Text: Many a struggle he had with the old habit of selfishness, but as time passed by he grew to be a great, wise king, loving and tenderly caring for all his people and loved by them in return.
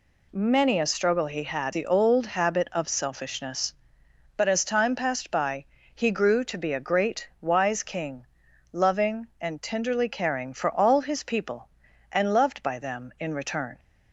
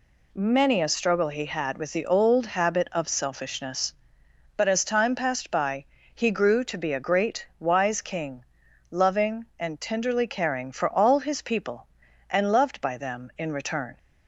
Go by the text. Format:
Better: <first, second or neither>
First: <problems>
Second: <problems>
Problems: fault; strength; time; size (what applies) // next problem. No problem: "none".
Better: second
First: skips "with"; at 1.7 s // pauses between "by" and "he"; slight; at 5.6 s; 0.32 s long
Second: pauses between "by" and "he"; slight; at 5.8 s; 0.32 s long